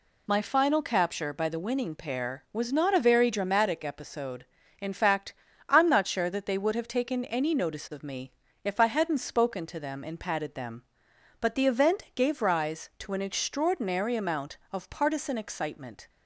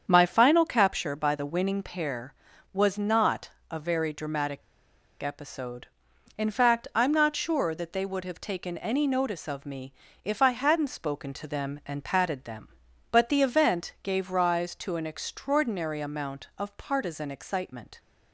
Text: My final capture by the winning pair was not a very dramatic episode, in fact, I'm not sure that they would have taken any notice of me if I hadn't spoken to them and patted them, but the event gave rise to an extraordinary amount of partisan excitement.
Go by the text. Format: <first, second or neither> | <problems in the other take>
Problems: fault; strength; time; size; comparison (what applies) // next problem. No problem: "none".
first | starts louder than the rest; strong; until 1.1 s; 7.5 dB // pauses between "not" and "a"; slight; at 3.4 s; 0.20 s long // pauses between "dramatic" and "episode"; noticeable; at 4.6 s; 0.59 s long // pauses between "me" and "if"; slight; at 9.9 s; 0.30 s long; slight in the first